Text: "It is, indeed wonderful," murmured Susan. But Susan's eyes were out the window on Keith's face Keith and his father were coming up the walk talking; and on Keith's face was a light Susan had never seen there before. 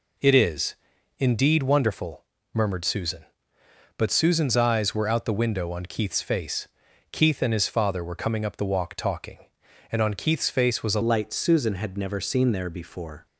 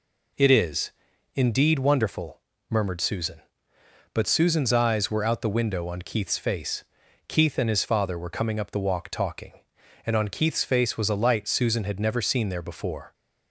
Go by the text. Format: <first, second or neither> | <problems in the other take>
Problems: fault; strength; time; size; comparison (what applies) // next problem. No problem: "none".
second | pauses between "face" and "Keith"; noticeable; at 6.6 s; 0.46 s long; noticeable in the second // changes voice at "light"; from 11.0 s on; 2.2 s long